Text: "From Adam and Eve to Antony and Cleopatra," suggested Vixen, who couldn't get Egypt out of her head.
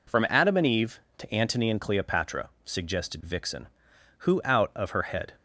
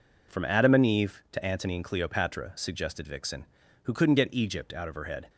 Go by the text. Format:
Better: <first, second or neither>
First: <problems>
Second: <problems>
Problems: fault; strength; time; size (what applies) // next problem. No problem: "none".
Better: second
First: skips "couldn't get Egypt"; at 4.4 s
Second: none